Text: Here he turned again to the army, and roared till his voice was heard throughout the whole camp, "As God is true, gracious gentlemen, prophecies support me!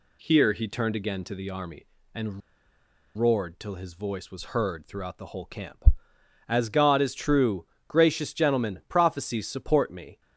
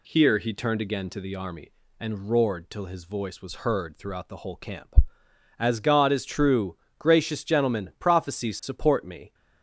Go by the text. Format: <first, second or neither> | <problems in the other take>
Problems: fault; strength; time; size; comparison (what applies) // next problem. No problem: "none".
second | pauses between "and" and "roared"; noticeable; at 2.4 s; 0.77 s long